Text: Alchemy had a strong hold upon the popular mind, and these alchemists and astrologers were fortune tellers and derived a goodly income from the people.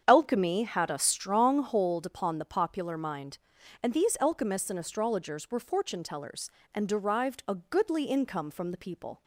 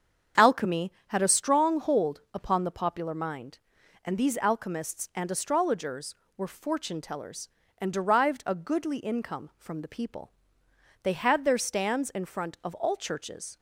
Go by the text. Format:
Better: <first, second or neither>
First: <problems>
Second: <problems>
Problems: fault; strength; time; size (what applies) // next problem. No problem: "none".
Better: first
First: starts louder than the rest; strong; until 1.0 s; 8 dB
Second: starts louder than the rest; strong; until 1.5 s; 7.5 dB // goes on to say "They had their stands in front of all churches"; strong; from 11.0 s on; 2.5 s long